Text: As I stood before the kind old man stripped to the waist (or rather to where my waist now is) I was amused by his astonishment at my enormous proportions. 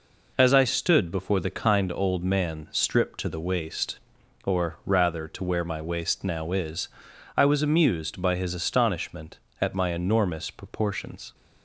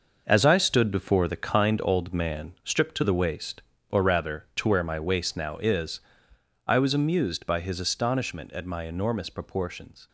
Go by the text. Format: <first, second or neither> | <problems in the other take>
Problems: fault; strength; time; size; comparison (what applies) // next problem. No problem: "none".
first | gets quieter; strong; throughout; 9.5 dB